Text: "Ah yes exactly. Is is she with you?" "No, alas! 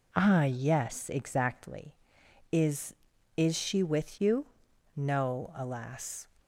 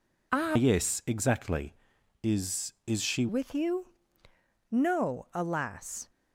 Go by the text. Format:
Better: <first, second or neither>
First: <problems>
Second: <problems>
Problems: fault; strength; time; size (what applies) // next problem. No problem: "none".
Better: first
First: none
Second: changes voice from "yes" to "she"; from 0.5 to 3.2 s; 2.7 s long